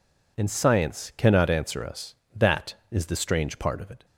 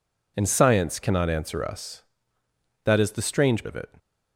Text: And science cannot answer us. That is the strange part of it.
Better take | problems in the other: first | skips "part"; at 3.6 s

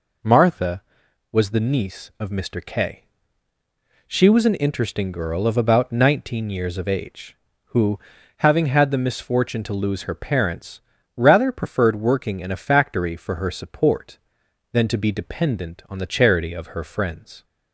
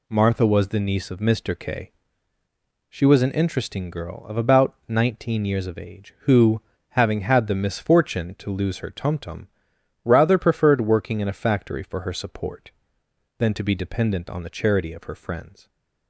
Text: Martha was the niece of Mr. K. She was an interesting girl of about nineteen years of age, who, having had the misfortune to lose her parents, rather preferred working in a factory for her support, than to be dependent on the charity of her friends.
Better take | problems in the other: first | says "tumtum" for "parents"; at 8.9 s

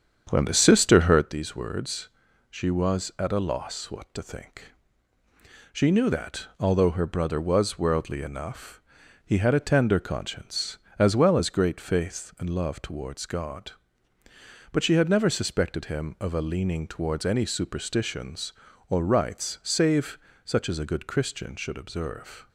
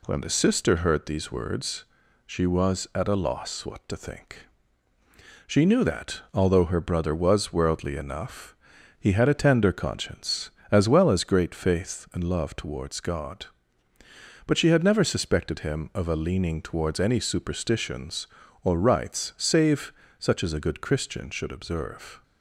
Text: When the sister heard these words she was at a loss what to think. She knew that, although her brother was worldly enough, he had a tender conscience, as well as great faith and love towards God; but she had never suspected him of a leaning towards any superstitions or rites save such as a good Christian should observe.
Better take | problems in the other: second | starts louder than the rest; strong; until 1.3 s; 8 dB // pauses between "words" and "she"; at 2.0 s; 0.40 s long; also in the second // pauses between "save" and "such"; slight; at 20.1 s; 0.26 s long; slight in the second

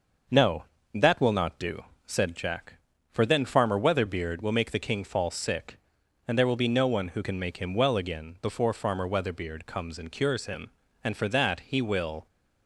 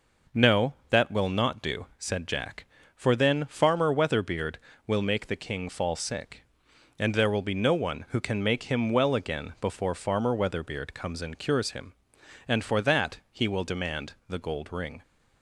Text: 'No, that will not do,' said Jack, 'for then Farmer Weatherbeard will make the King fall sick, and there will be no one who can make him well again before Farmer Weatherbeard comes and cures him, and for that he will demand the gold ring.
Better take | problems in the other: second | starts louder than the rest; noticeable; until 1.5 s; 6 dB // stops before "demand the gold ring"; at 12.2 s

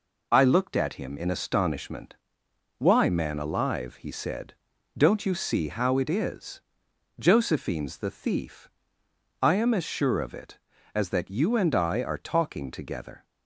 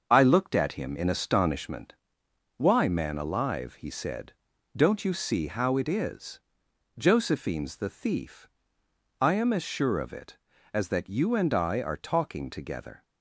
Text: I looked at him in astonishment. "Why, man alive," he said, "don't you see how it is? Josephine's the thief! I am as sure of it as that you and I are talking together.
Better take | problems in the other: first | starts louder than the rest; until 1.9 s; 6.5 dB

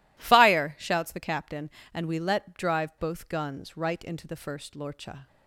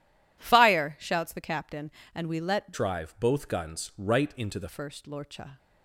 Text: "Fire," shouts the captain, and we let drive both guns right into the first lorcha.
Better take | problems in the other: first | changes voice from "drive" to "the"; from 2.7 to 4.6 s; 1.9 s long

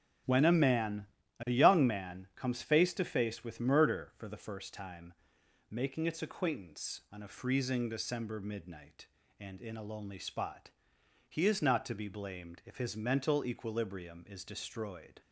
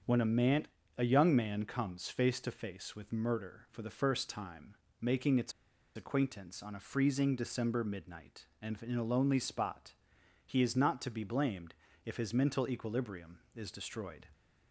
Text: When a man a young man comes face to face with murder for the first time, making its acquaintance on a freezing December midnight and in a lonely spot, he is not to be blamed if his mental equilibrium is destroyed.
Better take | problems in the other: first | starts louder than the rest; until 1.3 s; 7 dB; strong in the first // pauses between "man" and "a"; slight; at 0.6 s; 0.30 s long; slight in the first // pauses between "its" and "acquaintance"; at 5.5 s; 0.44 s long // pauses between "blamed" and "if"; slight; at 11.7 s; 0.32 s long

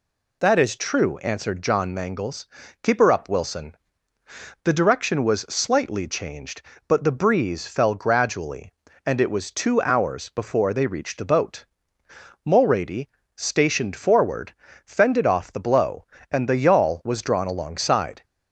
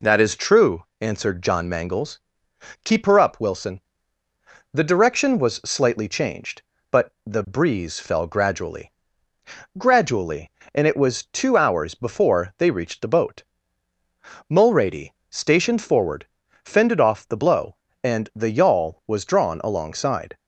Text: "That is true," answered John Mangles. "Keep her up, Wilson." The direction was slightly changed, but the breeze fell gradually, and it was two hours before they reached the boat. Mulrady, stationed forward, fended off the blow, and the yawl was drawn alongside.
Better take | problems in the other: first | says "gradually" twice; at 9.7 s

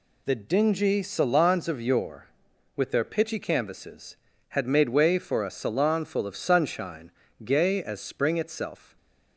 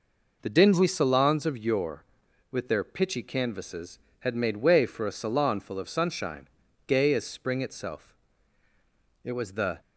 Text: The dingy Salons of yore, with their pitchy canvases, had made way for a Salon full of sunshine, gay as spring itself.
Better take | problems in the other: first | goes on to say "It was the"; from 9.2 s on; 0.56 s long

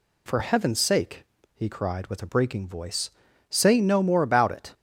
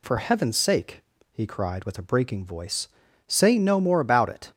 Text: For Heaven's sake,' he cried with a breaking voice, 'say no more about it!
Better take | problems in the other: neither | none

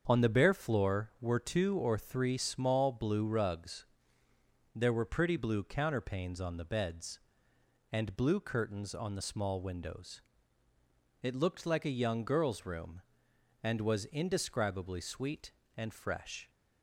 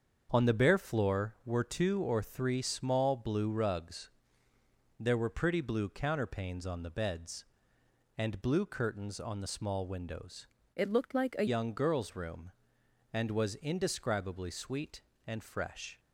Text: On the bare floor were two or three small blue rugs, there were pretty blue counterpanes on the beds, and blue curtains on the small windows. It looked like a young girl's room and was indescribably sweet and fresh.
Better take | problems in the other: first | starts louder than the rest; until 1.3 s; 7 dB; also in the first // changes voice from "It" to "a"; from 10.7 to 11.4 s; 0.7 s long

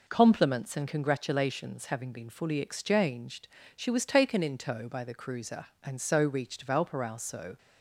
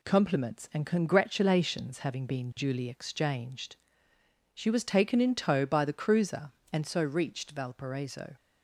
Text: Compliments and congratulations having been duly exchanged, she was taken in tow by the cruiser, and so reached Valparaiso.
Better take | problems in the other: second | says "fully" for "duly"; at 2.2 s

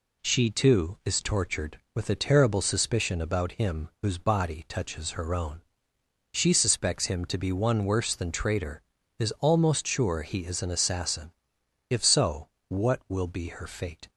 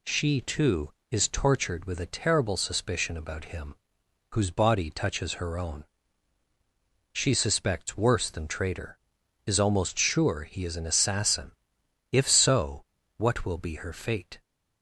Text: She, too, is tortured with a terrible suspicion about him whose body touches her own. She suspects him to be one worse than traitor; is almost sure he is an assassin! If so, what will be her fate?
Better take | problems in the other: first | pauses between "him" and "whose"; noticeable; at 3.7 s; 0.56 s long // skips "him to be one"; at 7.9 s

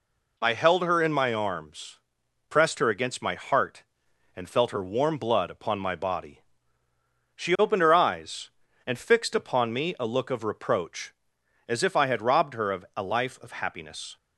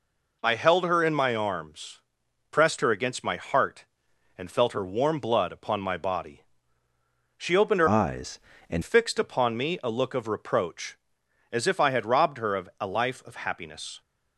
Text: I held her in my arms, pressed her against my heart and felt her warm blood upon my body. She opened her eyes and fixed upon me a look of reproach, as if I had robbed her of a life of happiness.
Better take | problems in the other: first | changes voice from "eyes" to "and"; from 7.8 to 8.8 s; 1.0 s long

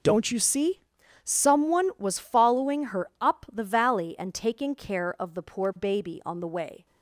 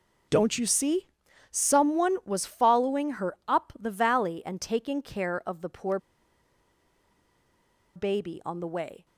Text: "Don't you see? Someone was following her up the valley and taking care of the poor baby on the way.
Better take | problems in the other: first | pauses between "poor" and "baby"; strong; at 5.9 s; 1.9 s long

